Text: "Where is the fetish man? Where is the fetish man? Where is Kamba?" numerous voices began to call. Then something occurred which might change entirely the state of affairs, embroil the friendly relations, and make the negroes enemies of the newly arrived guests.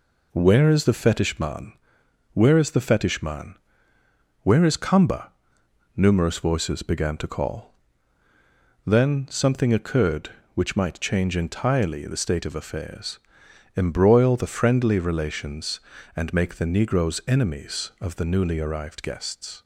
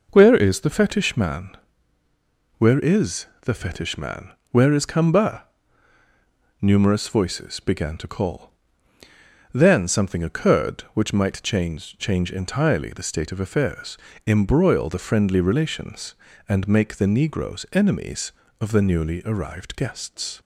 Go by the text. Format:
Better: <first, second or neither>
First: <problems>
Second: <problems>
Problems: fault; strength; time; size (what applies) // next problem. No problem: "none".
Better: first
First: none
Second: pauses between "is" and "the"; slight; at 3.2 s; 0.16 s long // says "change" twice; at 11.9 s